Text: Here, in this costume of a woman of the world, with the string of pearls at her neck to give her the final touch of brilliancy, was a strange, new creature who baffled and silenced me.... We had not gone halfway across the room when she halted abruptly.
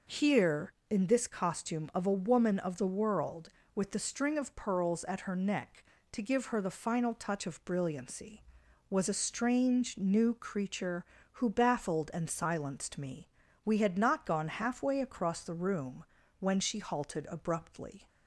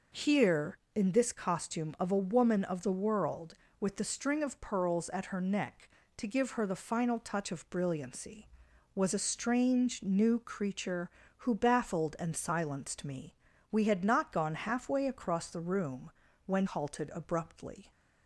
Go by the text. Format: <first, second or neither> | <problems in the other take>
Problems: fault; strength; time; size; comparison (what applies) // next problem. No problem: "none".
first | pauses between "room" and "when"; slight; at 16.1 s; 0.34 s long; slight in the first // skips "she"; at 16.6 s